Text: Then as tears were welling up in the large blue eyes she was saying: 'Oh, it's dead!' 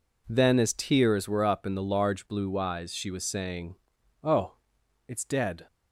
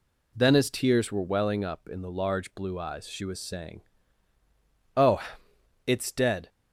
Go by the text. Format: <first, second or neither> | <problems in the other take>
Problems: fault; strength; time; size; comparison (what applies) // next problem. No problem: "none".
second | skips "welling"; at 1.4 s